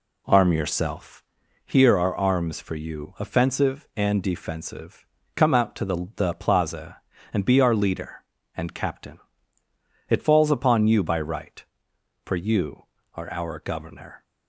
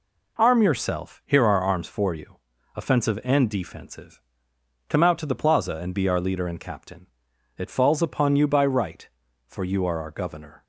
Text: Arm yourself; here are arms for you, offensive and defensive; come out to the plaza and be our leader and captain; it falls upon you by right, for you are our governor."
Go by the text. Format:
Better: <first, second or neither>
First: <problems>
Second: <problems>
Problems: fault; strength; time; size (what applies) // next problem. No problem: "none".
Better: second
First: says "the" twice; at 6.1 s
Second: none